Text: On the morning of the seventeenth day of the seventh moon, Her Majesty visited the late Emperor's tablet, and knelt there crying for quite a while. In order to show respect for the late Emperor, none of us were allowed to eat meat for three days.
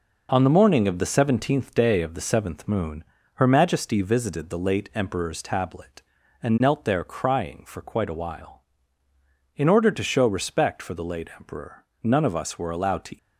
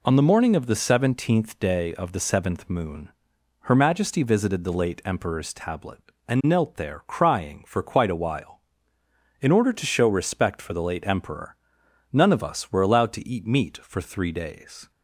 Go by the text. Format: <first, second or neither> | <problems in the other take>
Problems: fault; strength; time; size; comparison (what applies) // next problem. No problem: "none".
second | stops before "eat meat for three days"; at 13.1 s